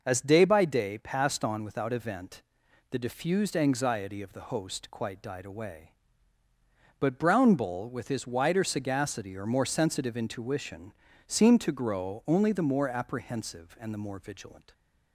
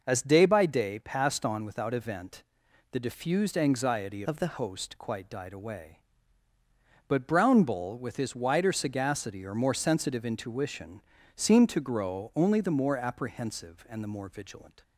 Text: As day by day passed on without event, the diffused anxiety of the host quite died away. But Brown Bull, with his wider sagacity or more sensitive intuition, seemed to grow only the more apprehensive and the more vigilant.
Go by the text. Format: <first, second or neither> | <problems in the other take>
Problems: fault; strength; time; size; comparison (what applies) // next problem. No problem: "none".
first | changes voice from "of" to "the"; from 4.2 to 4.5 s; 0.3 s long